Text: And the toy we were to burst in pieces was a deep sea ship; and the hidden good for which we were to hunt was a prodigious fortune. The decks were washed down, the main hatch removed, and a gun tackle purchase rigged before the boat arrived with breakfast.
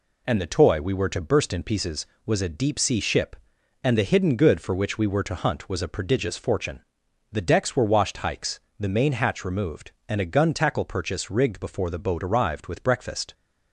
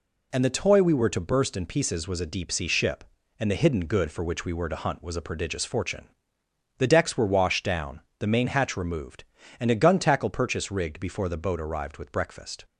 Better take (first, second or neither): second